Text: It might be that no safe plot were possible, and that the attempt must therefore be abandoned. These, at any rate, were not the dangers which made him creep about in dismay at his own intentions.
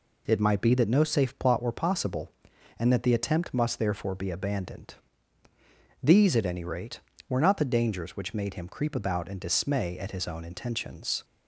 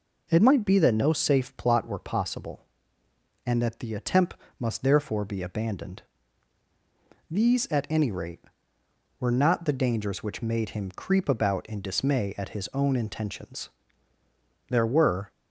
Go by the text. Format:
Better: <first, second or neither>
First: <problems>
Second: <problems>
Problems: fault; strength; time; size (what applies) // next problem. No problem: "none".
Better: first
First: none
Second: pauses between "attempt" and "must"; slight; at 4.3 s; 0.22 s long // goes on to say "There were"; noticeable; from 14.6 s on; 0.62 s long